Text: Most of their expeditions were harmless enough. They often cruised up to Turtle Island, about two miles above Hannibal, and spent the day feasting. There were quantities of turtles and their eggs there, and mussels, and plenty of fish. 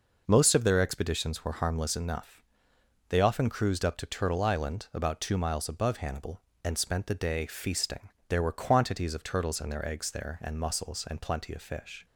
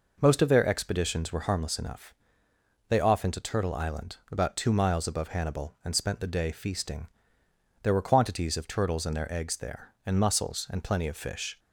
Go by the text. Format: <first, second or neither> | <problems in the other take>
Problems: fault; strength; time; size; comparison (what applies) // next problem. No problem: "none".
first | skips "cruised up"; at 3.3 s